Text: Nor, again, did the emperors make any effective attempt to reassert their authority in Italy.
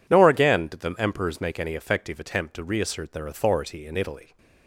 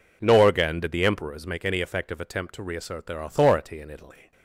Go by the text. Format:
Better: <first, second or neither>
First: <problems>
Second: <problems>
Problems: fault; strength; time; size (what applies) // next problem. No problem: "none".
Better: neither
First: none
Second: none